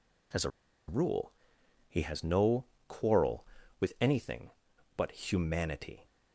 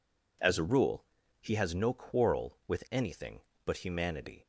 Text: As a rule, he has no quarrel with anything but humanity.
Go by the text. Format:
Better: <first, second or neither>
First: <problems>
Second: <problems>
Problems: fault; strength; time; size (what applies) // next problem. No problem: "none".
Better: second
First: pauses between "a" and "rule"; at 0.4 s; 0.38 s long // pauses between "no" and "quarrel"; slight; at 2.6 s; 0.22 s long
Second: none